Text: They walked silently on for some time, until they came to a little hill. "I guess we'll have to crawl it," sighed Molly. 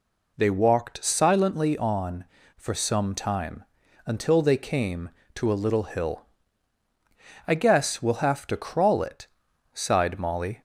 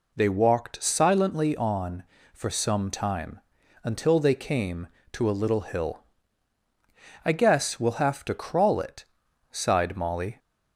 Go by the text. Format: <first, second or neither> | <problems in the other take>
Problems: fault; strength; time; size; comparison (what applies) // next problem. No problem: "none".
neither | none